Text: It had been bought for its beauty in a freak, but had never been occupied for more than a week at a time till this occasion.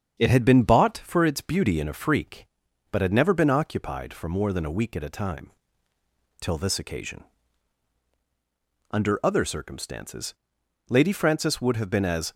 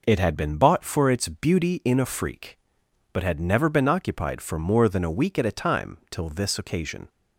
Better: second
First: starts louder than the rest; strong; until 1.2 s; 8 dB // pauses between "time" and "till"; noticeable; at 5.5 s; 0.90 s long // goes on to say "Under other circumstances Lady Frances would have been as"; strong; from 8.9 s on; 3.4 s long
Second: none

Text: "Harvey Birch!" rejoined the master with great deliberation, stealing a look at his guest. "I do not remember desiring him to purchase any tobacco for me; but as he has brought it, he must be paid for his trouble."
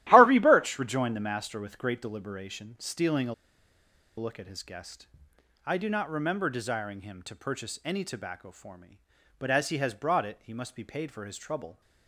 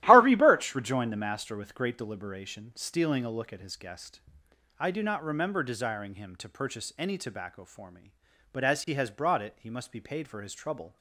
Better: second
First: starts louder than the rest; strong; until 1.0 s; 14 dB // pauses between "a" and "look"; noticeable; at 3.3 s; 0.83 s long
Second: starts louder than the rest; strong; until 1.0 s; 14 dB

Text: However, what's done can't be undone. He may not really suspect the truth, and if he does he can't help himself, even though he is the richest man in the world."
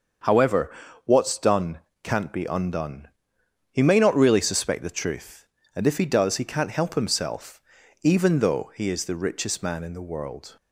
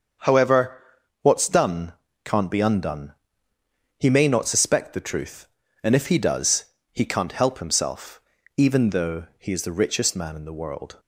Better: first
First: starts louder than the rest; until 1.5 s; 6.5 dB // pauses between "done" and "can't"; slight; at 1.8 s; 0.24 s long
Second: starts louder than the rest; until 1.6 s; 7 dB // pauses between "done" and "can't"; slight; at 1.9 s; 0.32 s long // skips "really"; at 4.4 s // pauses between "does" and "he"; slight; at 6.6 s; 0.26 s long

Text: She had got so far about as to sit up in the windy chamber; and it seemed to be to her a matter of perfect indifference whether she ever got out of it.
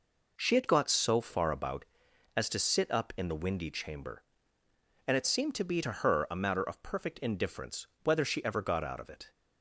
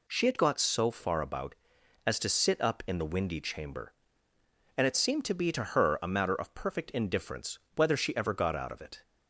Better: second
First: starts louder than the rest; noticeable; until 2.2 s; 4.5 dB // pauses between "indifference" and "whether"; slight; at 7.8 s; 0.16 s long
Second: pauses between "indifference" and "whether"; slight; at 7.5 s; 0.16 s long

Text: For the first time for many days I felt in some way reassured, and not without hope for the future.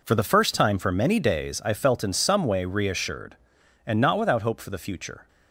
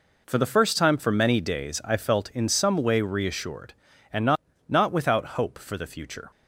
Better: first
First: none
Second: says "not" twice; at 4.6 s

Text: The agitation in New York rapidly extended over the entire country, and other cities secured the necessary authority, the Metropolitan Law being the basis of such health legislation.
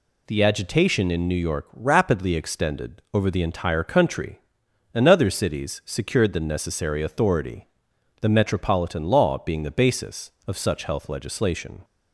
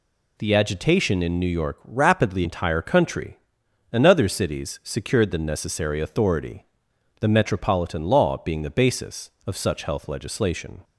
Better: first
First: none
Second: skips "extended over the"; at 2.4 s

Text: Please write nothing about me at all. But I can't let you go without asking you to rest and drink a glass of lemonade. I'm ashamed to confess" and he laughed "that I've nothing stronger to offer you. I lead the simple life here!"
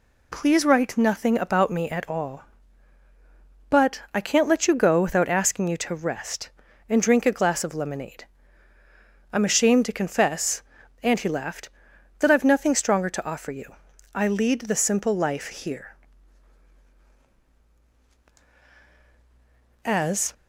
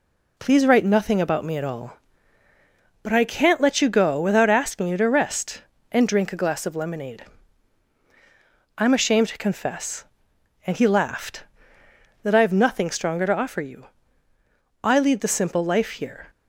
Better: second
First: goes on to say "As"; slight; from 19.8 s on; 0.48 s long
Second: none

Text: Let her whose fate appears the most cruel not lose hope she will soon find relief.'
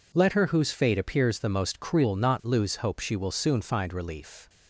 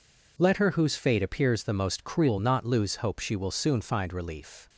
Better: neither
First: none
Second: none

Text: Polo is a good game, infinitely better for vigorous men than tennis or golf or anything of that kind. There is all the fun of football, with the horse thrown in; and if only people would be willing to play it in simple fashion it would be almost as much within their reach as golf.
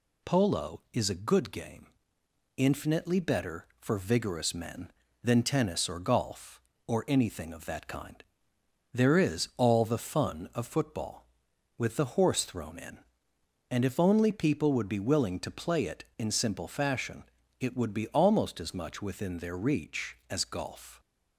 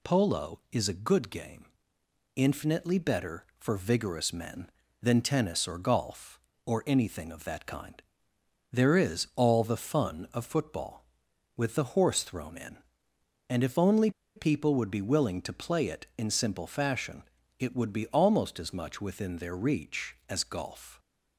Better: first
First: pauses between "fashion" and "it"; slight; at 17.2 s; 0.36 s long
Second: pauses between "only" and "people"; slight; at 14.0 s; 0.26 s long // pauses between "fashion" and "it"; slight; at 17.2 s; 0.36 s long

